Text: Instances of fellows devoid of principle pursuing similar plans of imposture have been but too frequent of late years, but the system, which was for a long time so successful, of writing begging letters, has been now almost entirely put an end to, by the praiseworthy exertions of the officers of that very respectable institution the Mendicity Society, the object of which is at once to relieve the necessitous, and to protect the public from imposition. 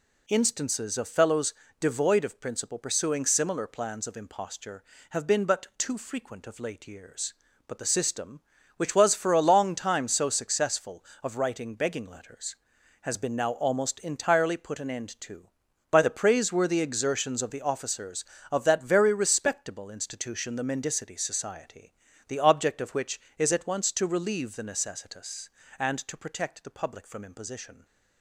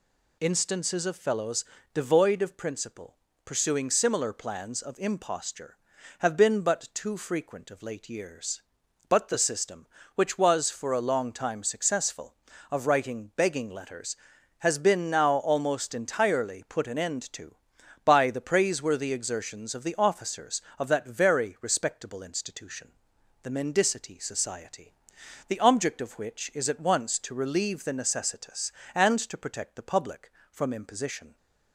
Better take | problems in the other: first | pauses between "fellows" and "devoid"; slight; at 1.6 s; 0.30 s long; slight in the first // pauses between "principle" and "pursuing"; slight; at 3.1 s; 0.28 s long // skips "so"; at 11.6 s // pauses between "institution" and "the"; noticeable; at 22.9 s; 0.52 s long

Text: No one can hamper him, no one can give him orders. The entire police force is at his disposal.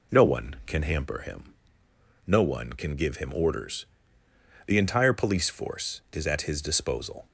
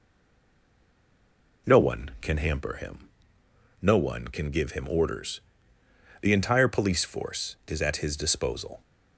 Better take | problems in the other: first | stays silent before the first word; noticeable; until 1.6 s; 1.6 s long

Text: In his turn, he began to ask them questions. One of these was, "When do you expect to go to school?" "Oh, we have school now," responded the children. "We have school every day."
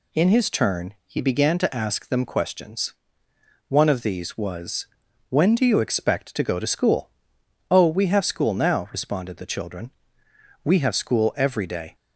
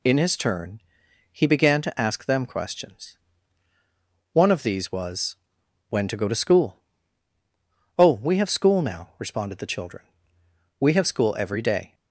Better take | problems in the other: first | skips "do you expect"; at 6.0 s

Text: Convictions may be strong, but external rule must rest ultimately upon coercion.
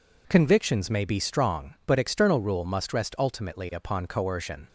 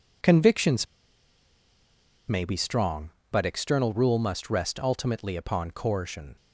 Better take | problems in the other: first | pauses between "Convictions" and "may"; strong; at 0.8 s; 1.4 s long

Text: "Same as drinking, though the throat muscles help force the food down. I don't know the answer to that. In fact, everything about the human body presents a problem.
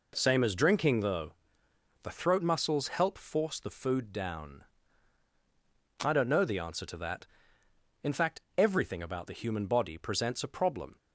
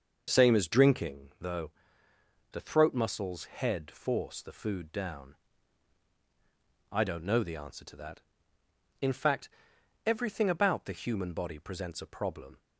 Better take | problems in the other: first | starts louder than the rest; until 1.2 s; 6 dB // pauses between "though" and "the"; noticeable; at 1.7 s; 0.80 s long; noticeable in the first // says "head" for "help"; at 3.4 s

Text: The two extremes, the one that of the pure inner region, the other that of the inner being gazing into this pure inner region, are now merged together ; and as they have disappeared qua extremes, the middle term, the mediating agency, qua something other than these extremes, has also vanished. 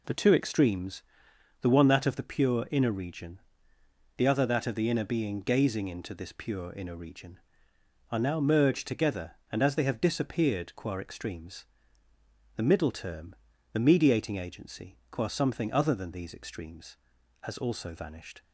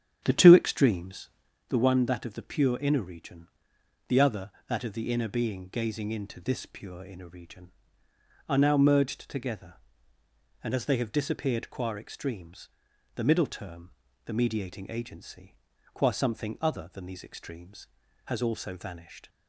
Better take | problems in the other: first | starts louder than the rest; strong; until 1.5 s; 9.5 dB

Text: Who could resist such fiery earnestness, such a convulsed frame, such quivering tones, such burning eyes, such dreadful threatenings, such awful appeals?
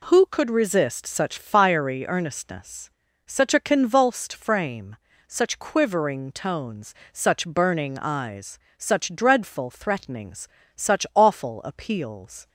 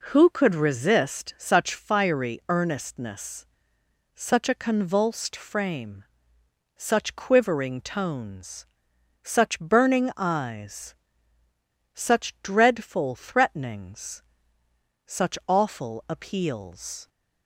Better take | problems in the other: neither | none

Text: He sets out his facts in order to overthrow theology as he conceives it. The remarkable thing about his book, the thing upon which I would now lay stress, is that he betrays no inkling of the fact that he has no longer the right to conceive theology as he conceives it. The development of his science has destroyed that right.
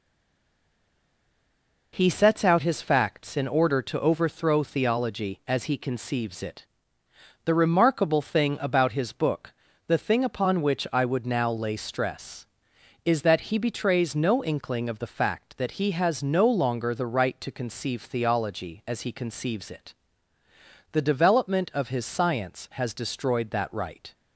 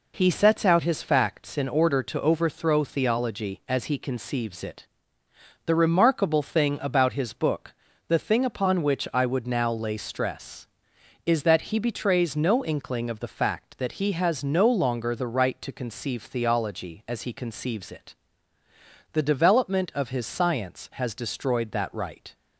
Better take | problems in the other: second | stays silent before the first word; noticeable; until 1.9 s; 1.9 s long

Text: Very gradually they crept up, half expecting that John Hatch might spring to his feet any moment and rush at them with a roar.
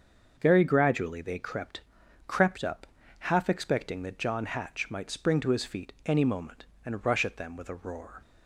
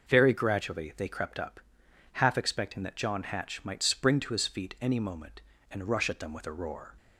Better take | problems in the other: second | starts louder than the rest; until 1.3 s; 6.5 dB // says "crept" twice; at 2.2 s

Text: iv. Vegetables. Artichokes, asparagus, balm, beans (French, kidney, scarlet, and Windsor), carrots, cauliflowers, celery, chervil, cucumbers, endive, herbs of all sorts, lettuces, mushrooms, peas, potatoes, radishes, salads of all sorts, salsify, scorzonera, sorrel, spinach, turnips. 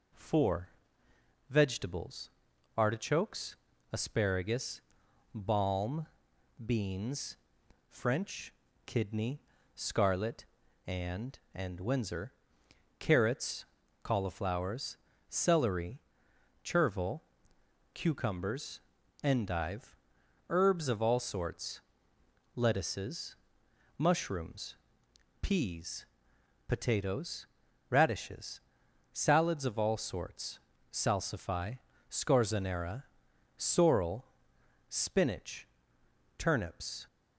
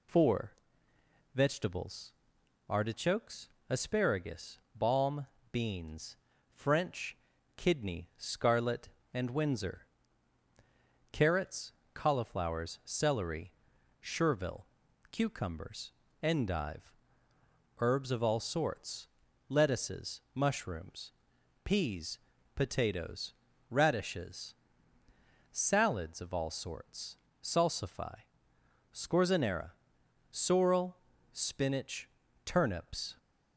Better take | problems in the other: second | says "and" twice; at 11.5 s

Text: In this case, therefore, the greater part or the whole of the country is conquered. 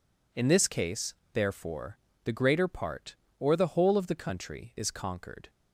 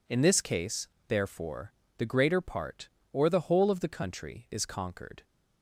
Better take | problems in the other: neither | none

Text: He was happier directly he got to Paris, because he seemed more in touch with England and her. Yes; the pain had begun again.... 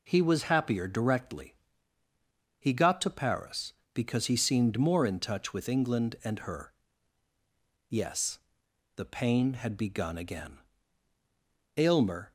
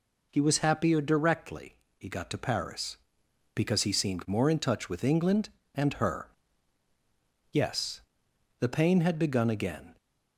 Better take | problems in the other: second | pauses between "directly" and "he"; at 1.5 s; 1.0 s long; slight in the second // goes on to say "Aylmer"; from 11.7 s on; 0.56 s long

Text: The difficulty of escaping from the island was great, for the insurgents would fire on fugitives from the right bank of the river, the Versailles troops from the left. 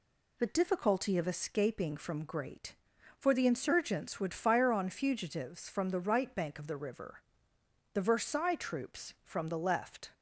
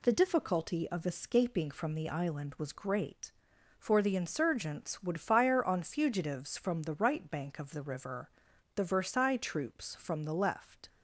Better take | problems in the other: second | skips "the island was"; at 2.2 s

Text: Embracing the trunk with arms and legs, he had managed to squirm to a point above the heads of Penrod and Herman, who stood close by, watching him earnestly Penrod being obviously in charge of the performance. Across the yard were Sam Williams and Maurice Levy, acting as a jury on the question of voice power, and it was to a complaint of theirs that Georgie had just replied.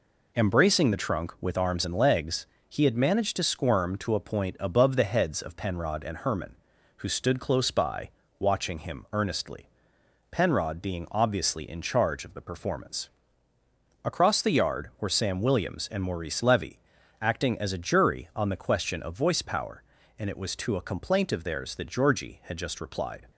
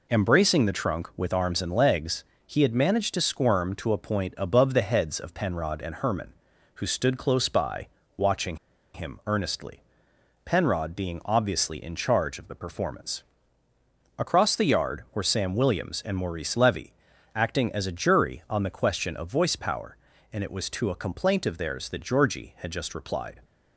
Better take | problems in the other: first | pauses between "watching" and "him"; at 8.5 s; 0.37 s long // pauses between "earnestly" and "Penrod"; noticeable; at 9.8 s; 0.64 s long; noticeable in the first

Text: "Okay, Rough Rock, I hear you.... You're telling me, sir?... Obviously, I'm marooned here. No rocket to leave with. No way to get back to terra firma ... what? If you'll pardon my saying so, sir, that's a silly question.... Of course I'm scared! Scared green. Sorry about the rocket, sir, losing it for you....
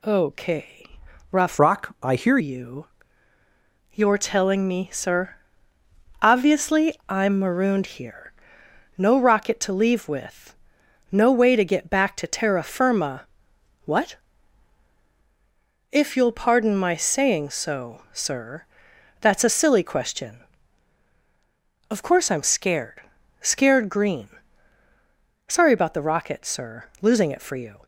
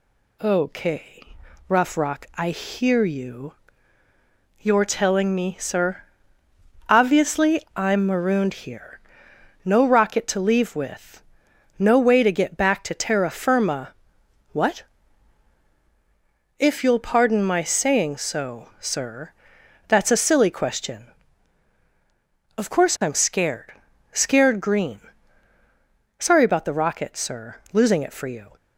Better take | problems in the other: second | changes voice from "Rock" to "hear"; from 1.5 to 2.3 s; 0.8 s long

